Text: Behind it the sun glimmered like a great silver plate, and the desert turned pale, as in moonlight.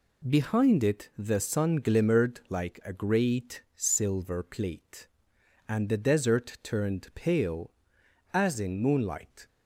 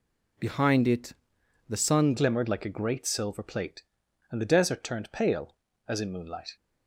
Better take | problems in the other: first | pauses between "it" and "the"; noticeable; at 1.1 s; 0.54 s long // changes voice at "glimmered"; from 2.1 s on; 4.4 s long

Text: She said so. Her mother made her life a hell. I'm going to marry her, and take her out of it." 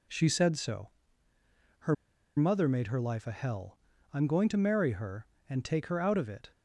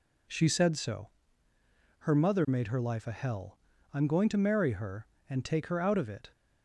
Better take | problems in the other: second | pauses between "Her" and "mother"; at 1.9 s; 0.42 s long

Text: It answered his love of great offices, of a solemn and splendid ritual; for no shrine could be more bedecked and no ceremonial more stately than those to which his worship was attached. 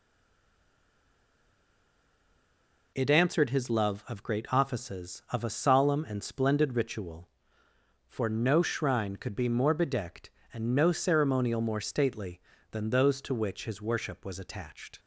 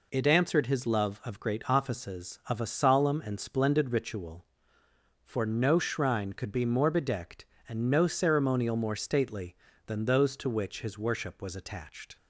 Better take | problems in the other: second | stays silent before the first word; strong; until 2.9 s; 2.9 s long

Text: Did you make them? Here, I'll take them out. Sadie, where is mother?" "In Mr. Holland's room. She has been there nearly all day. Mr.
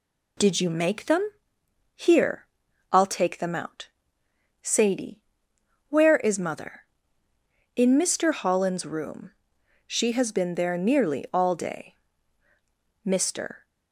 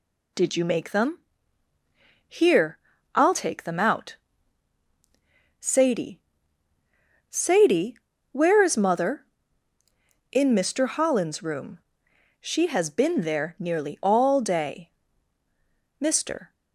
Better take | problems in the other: first | says "Sadie" twice; at 7.2 s

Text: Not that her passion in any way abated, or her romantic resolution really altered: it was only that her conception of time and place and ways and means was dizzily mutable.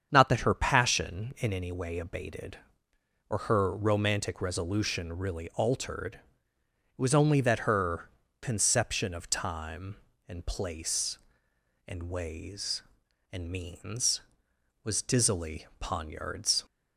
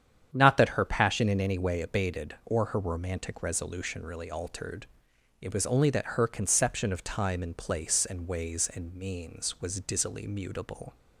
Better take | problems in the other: second | starts louder than the rest; strong; until 1.1 s; 7.5 dB; strong in the second // pauses between "her" and "conception"; slight; at 8.0 s; 0.32 s long // says "poniards" for "mutable"; at 15.7 s

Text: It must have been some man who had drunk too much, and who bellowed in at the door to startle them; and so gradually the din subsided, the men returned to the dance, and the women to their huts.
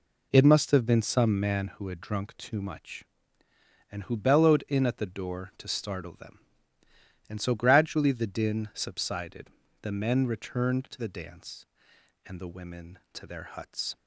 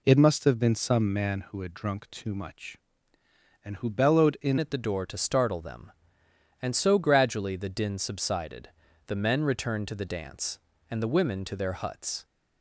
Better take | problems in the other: first | changes voice at "at"; from 4.5 s on; 7.7 s long

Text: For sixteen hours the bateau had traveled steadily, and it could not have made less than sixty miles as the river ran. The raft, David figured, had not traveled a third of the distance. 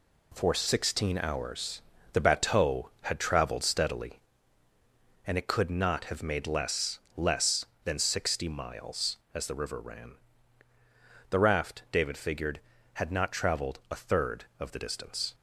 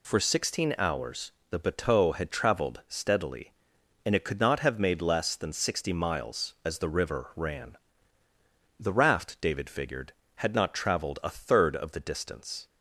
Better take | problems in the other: second | pauses between "hours" and "the"; slight; at 1.8 s; 0.30 s long; slight in the second // says "less" twice; at 7.1 s

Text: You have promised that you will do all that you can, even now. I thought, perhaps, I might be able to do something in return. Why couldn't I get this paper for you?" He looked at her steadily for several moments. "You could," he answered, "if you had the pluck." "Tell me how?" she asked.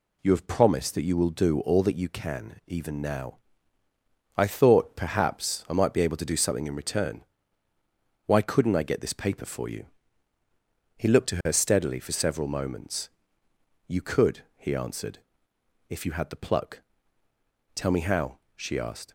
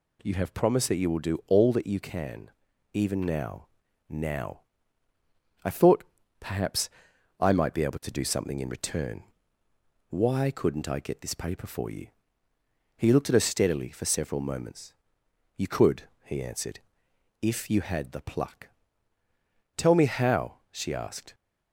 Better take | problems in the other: first | says "now" twice; at 4.1 s

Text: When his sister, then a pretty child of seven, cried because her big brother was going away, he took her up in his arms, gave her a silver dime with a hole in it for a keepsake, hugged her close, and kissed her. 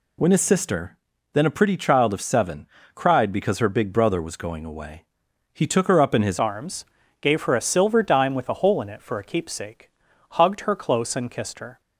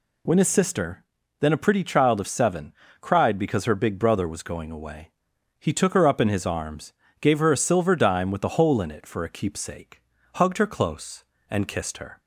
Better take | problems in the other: second | changes voice at "arms"; from 6.3 s on; 5.5 s long

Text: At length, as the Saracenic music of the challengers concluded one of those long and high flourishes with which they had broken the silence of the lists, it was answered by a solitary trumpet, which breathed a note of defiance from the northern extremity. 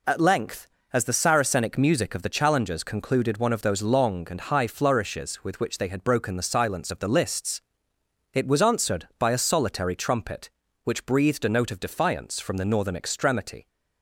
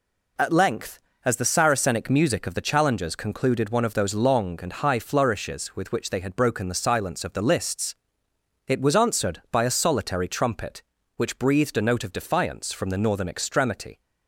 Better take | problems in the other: neither | none

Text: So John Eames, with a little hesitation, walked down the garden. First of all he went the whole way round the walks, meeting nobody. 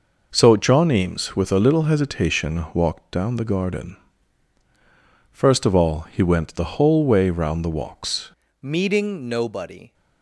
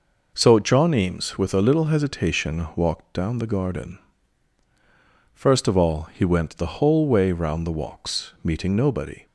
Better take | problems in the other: second | changes voice at "meeting"; from 8.6 s on; 1.3 s long

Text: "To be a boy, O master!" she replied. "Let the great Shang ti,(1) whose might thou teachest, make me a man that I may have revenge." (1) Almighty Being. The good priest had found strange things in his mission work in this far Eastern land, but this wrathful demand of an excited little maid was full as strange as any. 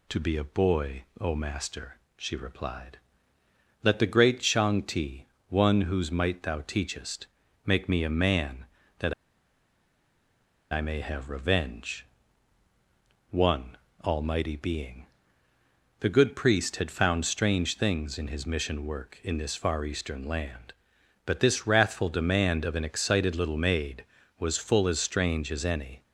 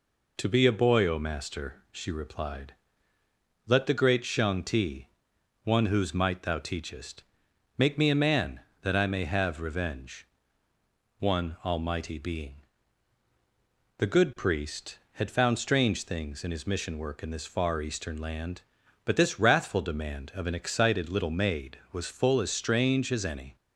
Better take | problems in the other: second | pauses between "that" and "I"; strong; at 9.1 s; 1.5 s long

